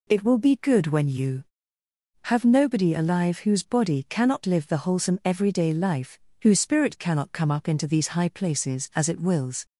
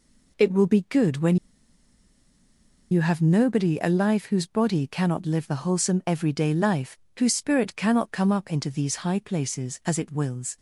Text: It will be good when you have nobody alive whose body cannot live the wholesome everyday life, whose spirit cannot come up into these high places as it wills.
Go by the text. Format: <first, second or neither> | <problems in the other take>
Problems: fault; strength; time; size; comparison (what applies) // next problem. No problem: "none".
first | pauses between "when" and "you"; strong; at 1.3 s; 1.5 s long